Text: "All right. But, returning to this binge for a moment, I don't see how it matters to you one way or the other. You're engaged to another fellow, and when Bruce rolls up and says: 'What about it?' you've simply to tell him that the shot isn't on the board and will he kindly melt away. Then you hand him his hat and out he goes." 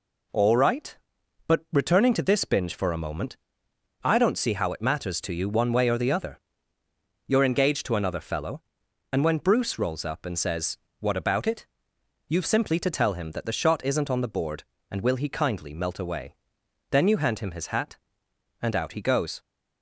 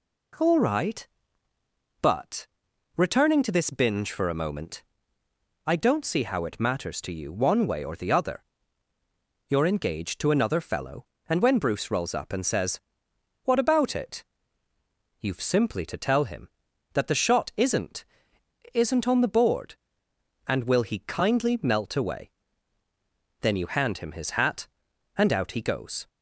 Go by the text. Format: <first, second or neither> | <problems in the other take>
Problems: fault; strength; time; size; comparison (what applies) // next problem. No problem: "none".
first | says "isn't" twice; at 18.7 s